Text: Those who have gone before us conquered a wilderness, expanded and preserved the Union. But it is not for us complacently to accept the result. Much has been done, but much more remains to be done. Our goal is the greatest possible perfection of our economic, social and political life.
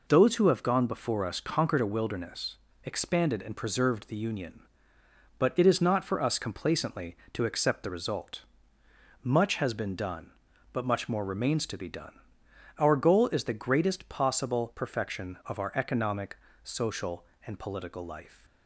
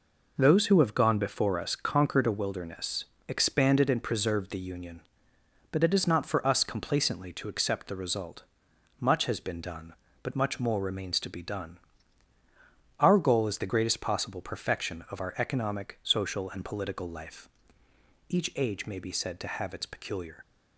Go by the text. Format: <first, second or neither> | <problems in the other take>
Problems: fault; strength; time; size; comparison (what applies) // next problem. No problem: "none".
first | goes on to say "Each age may be said to have its peculiar"; strong; from 18.2 s on; 2.1 s long